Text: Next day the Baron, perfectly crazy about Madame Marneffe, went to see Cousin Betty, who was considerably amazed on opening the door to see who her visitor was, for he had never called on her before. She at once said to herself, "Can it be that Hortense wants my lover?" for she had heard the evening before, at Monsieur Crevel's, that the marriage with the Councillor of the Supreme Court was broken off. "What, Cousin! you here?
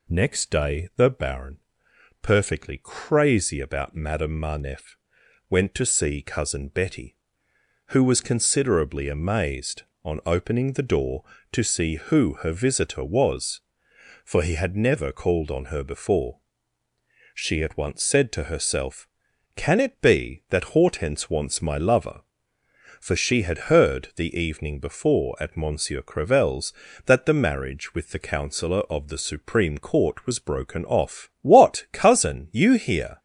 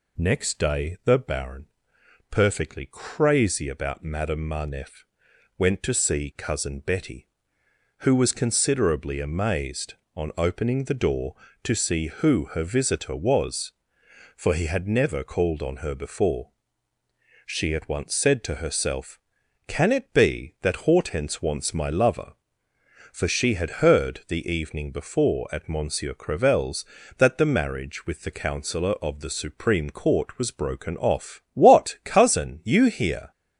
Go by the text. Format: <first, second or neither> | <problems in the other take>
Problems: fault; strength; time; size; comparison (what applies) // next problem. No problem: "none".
neither | none